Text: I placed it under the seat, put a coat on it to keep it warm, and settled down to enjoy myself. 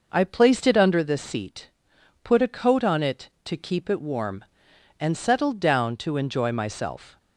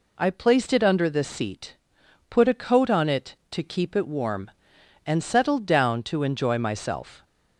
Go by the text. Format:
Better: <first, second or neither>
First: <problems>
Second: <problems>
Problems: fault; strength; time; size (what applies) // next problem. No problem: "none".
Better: second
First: starts louder than the rest; noticeable; until 1.1 s; 5.5 dB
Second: none